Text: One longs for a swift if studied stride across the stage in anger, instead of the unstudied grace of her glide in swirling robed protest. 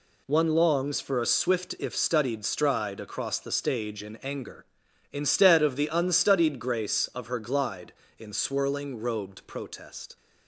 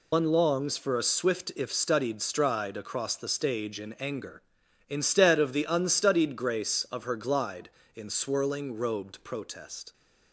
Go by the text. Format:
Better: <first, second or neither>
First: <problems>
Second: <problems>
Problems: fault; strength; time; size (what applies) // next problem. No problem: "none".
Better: first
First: none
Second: loses the start of "One"; at 0.1 s; 100 ms